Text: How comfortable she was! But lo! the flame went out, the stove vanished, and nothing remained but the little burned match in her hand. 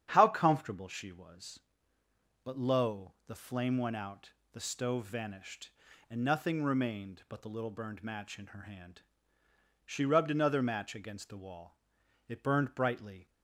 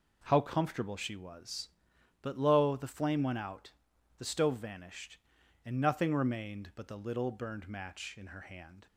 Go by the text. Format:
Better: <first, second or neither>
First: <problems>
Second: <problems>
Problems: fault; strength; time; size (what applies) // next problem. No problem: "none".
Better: second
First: starts louder than the rest; strong; until 1.1 s; 9 dB // goes on to say "She rubbed another match against the wall It burned brightly"; strong; from 9.8 s on; 3.4 s long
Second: none